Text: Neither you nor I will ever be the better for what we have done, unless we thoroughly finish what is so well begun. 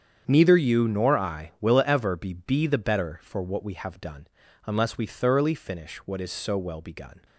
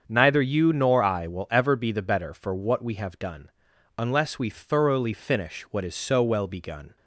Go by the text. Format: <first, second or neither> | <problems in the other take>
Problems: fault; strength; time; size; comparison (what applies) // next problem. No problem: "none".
second | starts louder than the rest; strong; until 1.2 s; 8 dB; strong in the second // says "be" twice; at 2.3 s